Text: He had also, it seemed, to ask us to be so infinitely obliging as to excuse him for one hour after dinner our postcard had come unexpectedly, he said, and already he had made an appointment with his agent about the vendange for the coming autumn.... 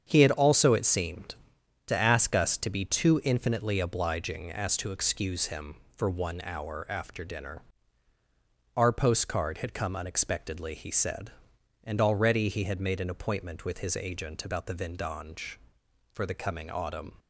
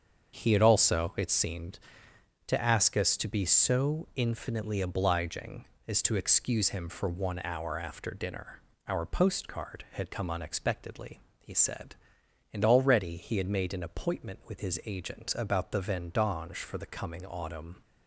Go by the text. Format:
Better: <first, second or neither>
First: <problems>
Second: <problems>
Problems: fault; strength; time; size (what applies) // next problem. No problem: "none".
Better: second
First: starts louder than the rest; strong; until 1.0 s; 7.5 dB // says "too" for "so"; at 2.8 s // pauses between "dinner" and "our"; at 7.6 s; 1.1 s long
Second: starts louder than the rest; until 1.3 s; 7 dB // pauses between "dinner" and "our"; slight; at 8.6 s; 0.26 s long